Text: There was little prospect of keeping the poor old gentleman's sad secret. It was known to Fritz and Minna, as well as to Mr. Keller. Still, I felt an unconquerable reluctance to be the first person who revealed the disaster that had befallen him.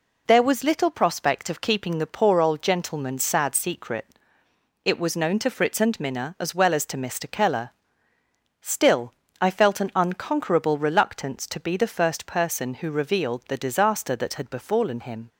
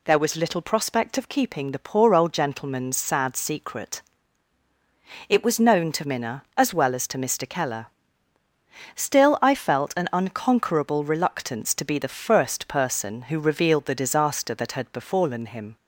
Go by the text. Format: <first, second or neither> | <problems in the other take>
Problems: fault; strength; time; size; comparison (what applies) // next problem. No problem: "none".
first | skips "Fritz and"; at 6.0 s